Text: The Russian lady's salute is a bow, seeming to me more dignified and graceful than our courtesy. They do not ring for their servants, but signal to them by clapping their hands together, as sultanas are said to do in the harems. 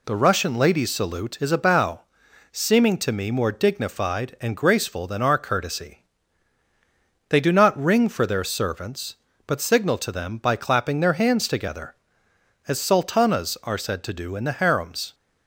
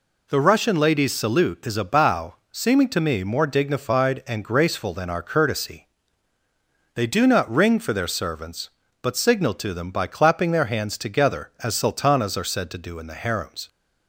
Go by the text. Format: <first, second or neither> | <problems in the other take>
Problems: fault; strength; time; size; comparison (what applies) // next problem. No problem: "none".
neither | none